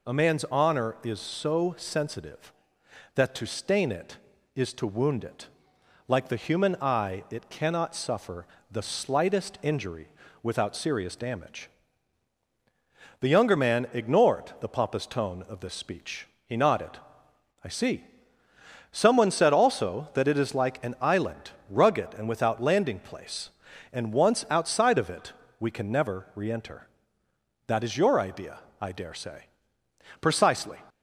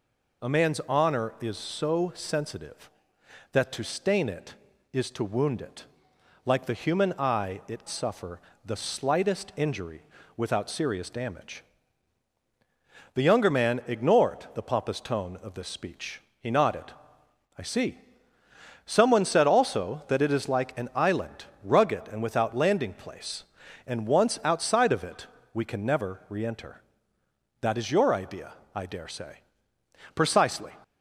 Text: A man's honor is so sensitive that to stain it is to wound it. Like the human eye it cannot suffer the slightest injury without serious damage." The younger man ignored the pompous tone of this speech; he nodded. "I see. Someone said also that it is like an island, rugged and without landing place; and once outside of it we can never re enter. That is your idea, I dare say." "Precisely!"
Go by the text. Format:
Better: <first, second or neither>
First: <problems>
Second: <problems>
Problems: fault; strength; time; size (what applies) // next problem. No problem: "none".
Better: first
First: pauses between "suffer" and "the"; slight; at 8.4 s; 0.26 s long // pauses between "injury" and "without"; slight; at 10.0 s; 0.36 s long // pauses between "it" and "we"; slight; at 25.3 s; 0.28 s long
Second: skips "cannot"; at 7.8 s // pauses between "suffer" and "the"; slight; at 8.3 s; 0.26 s long // pauses between "injury" and "without"; slight; at 10.0 s; 0.36 s long // pauses between "it" and "we"; slight; at 25.2 s; 0.28 s long